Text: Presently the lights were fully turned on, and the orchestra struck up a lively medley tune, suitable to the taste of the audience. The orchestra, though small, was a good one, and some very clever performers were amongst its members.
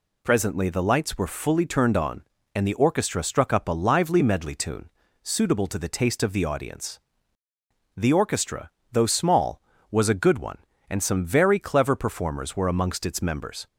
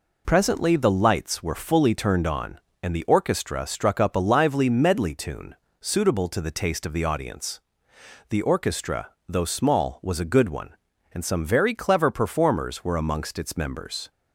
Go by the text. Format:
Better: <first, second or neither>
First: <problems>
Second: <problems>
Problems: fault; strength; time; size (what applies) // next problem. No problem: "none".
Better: neither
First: none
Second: none